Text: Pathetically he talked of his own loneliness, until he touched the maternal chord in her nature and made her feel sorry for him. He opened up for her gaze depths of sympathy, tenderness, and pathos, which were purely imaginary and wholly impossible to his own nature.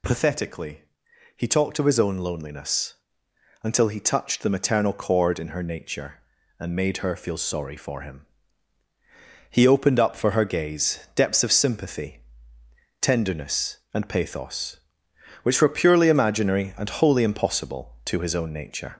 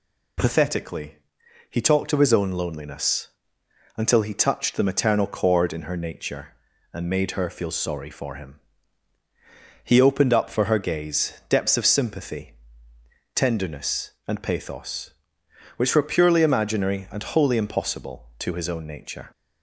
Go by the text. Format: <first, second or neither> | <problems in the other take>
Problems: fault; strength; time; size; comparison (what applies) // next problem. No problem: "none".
second | gets louder; slight; throughout; 2 dB // pauses between "Pathetically" and "he"; noticeable; at 0.8 s; 0.52 s long; noticeable in the second // pauses between "gaze" and "depths"; slight; at 10.9 s; 0.16 s long; slight in the second